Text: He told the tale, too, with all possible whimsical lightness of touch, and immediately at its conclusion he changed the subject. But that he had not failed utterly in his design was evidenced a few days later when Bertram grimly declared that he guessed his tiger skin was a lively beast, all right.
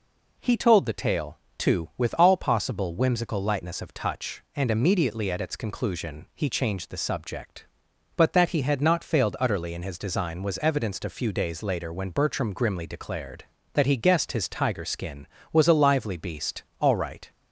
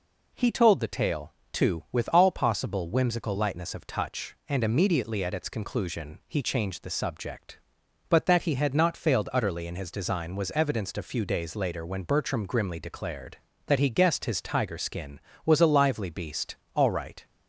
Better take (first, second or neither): neither